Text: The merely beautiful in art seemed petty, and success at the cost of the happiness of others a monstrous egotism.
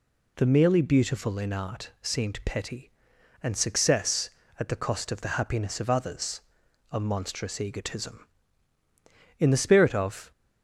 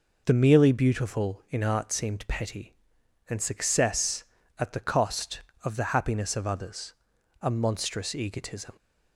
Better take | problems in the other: second | pauses between "others" and "a"; noticeable; at 6.4 s; 0.50 s long; noticeable in the second // goes on to say "In the spirit of"; noticeable; from 9.3 s on; 0.92 s long

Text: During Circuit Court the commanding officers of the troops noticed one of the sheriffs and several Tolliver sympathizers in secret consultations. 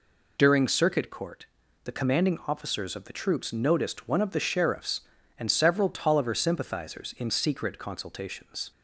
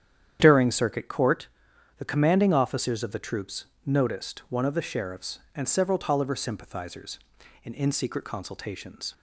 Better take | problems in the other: first | starts louder than the rest; strong; until 1.4 s; 9.5 dB // pauses between "Court" and "the"; noticeable; at 1.4 s; 0.50 s long; also in the first // pauses between "troops" and "noticed"; slight; at 3.6 s; 0.18 s long // says "in" twice; at 7.7 s

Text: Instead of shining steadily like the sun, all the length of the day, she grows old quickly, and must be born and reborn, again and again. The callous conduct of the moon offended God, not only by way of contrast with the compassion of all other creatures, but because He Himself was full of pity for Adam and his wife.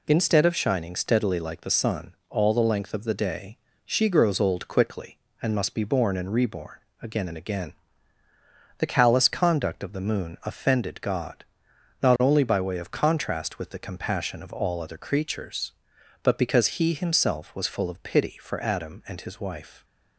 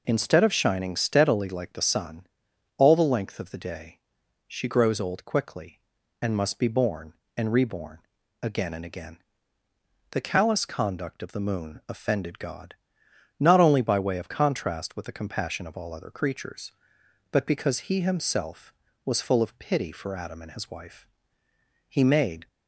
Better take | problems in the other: first | goes on to say "He made"; from 21.8 s on; 0.60 s long

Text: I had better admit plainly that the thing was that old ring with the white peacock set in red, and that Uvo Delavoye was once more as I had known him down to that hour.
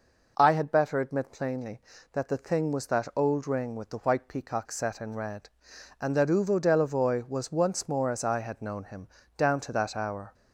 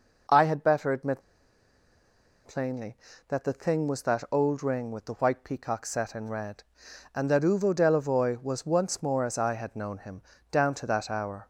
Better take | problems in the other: first | pauses between "admit" and "plainly"; at 1.2 s; 1.2 s long // pauses between "him" and "down"; slight; at 10.2 s; 0.30 s long; slight in the first

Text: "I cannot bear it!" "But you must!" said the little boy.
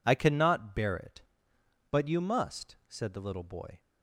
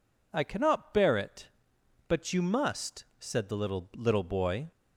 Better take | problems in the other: first | says "little" twice; at 3.9 s

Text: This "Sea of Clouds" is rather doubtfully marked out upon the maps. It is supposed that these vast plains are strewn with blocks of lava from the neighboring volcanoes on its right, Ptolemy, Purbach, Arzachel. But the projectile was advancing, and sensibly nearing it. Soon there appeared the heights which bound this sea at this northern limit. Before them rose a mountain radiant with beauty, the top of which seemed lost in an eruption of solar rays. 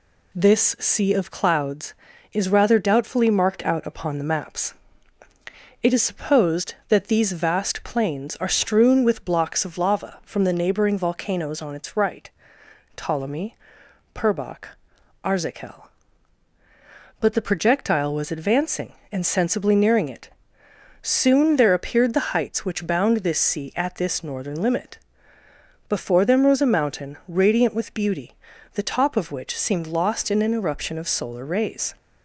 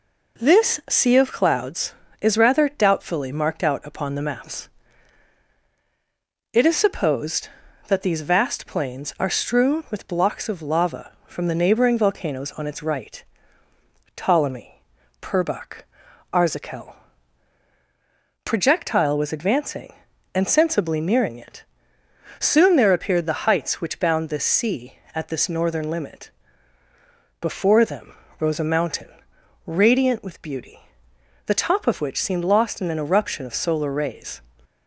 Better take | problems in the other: first | skips "But the"; at 17.6 s // pauses between "them" and "rose"; slight; at 28.1 s; 0.26 s long // pauses between "mountain" and "radiant"; noticeable; at 29.0 s; 0.60 s long

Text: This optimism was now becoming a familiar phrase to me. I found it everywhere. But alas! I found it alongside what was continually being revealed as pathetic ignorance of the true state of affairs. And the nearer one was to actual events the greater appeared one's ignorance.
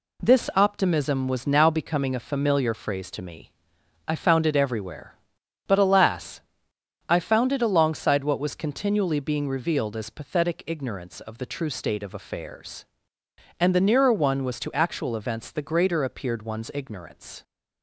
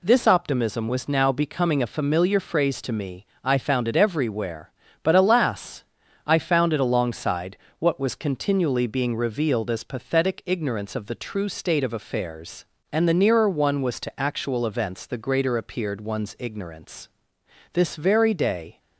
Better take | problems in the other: first | pauses between "alongside" and "what"; slight; at 7.5 s; 0.24 s long // goes on to say "This very day"; noticeable; from 17.7 s on; 1.0 s long

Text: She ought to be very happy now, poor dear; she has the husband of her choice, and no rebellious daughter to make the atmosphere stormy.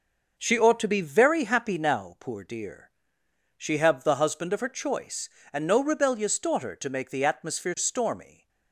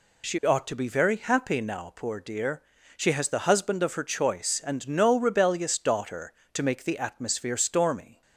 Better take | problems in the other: second | says "have" for "has"; at 3.7 s

